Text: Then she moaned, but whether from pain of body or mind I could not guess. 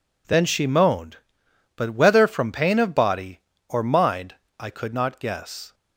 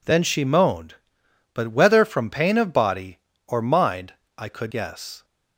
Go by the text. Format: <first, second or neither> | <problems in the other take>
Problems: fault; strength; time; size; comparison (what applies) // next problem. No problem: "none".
first | pauses between "mind" and "I"; slight; at 4.1 s; 0.22 s long; slight in the first // skips "not"; at 4.7 s